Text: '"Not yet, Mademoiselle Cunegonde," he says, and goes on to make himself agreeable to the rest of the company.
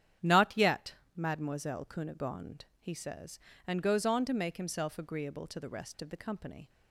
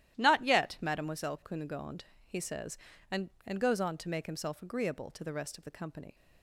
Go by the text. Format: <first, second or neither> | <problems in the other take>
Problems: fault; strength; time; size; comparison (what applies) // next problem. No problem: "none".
first | starts louder than the rest; strong; until 1.2 s; 13 dB; strong in the first // says "and" twice; at 3.4 s